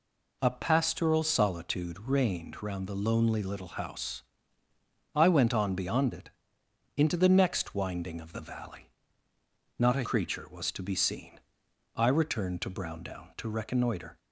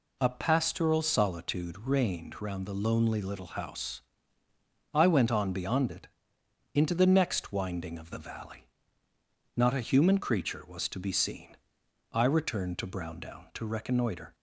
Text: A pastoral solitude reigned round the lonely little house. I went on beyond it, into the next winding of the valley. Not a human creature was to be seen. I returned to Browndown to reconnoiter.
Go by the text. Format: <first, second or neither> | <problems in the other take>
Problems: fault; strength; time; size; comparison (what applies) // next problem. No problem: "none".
second | skips "human"; at 10.0 s